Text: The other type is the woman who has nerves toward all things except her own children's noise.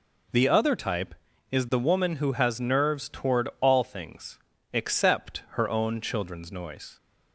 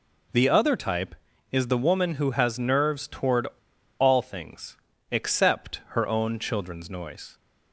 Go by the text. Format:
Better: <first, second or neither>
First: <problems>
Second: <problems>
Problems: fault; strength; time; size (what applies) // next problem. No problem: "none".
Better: first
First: pauses between "things" and "except"; slight; at 4.3 s; 0.34 s long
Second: pauses between "toward" and "all"; noticeable; at 3.4 s; 0.52 s long // pauses between "things" and "except"; slight; at 4.7 s; 0.34 s long